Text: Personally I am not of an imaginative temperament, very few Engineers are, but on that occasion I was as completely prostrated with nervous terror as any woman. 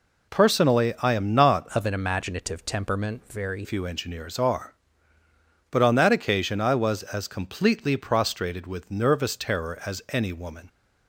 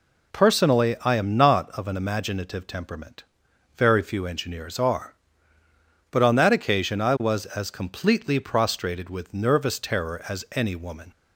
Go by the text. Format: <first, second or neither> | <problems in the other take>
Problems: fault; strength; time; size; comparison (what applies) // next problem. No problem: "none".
second | changes voice from "of" to "very"; from 1.7 to 3.6 s; 1.9 s long